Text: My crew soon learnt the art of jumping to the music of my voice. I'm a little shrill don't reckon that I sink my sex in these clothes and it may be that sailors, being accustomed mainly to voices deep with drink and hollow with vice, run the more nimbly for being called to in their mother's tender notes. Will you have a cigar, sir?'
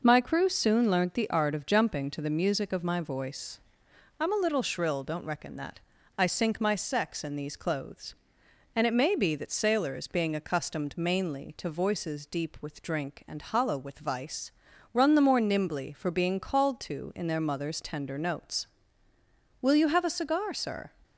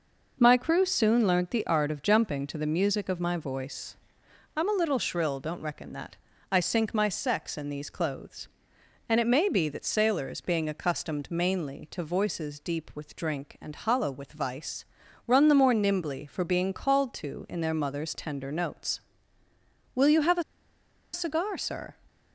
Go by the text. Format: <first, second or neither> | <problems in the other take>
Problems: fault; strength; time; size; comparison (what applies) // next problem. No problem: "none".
first | pauses between "that" and "I"; slight; at 6.1 s; 0.36 s long; also in the first // pauses between "a" and "cigar"; noticeable; at 20.4 s; 0.71 s long